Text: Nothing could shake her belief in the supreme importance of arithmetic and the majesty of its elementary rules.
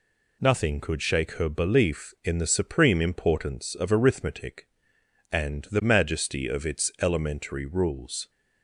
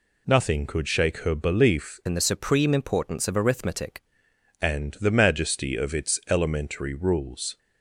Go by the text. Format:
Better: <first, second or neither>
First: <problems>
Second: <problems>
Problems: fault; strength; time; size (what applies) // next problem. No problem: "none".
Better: first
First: none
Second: changes voice from "in" to "arithmetic"; from 2.0 to 4.0 s; 2.0 s long